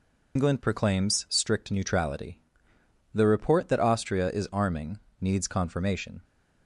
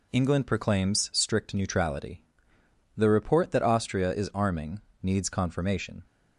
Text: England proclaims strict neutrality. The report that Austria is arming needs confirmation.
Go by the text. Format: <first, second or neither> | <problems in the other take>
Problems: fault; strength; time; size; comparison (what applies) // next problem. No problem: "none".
second | loses the start of "England"; at 0.3 s; 110 ms // pauses between "arming" and "needs"; slight; at 4.9 s; 0.22 s long; slight in the second